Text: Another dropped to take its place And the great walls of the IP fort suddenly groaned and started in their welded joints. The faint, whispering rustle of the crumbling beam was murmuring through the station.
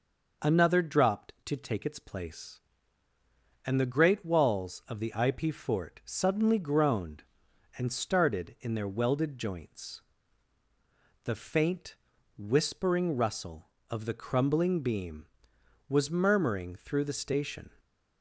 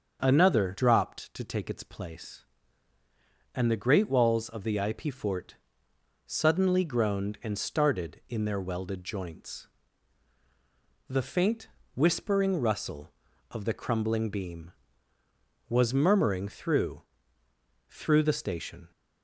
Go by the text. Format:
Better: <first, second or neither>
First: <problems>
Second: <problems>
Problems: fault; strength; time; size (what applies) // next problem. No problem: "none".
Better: first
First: none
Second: starts louder than the rest; until 1.2 s; 7 dB // pauses between "fort" and "suddenly"; noticeable; at 5.5 s; 0.72 s long // says "through" twice; at 17.8 s